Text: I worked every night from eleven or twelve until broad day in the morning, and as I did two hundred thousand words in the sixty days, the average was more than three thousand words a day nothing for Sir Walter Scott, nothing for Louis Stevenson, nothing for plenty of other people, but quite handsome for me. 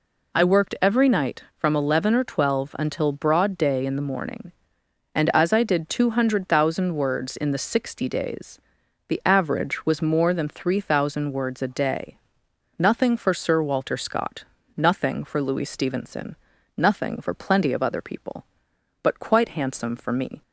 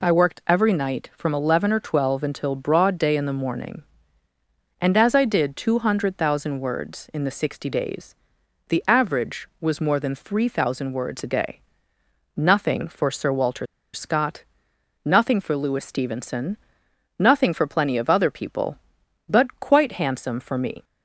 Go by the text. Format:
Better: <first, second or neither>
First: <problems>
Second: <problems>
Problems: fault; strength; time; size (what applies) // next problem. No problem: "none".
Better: first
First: pauses between "day" and "nothing"; noticeable; at 12.1 s; 0.60 s long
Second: pauses between "day" and "nothing"; noticeable; at 11.5 s; 0.76 s long // pauses between "Walter" and "Scott"; slight; at 13.6 s; 0.27 s long